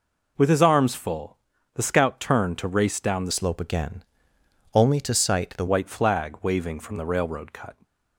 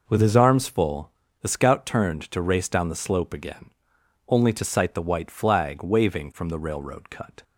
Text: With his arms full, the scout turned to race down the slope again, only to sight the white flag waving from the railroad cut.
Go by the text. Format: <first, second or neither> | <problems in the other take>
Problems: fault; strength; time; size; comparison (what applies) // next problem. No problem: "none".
second | changes voice from "slope" to "the"; from 3.3 to 5.6 s; 2.3 s long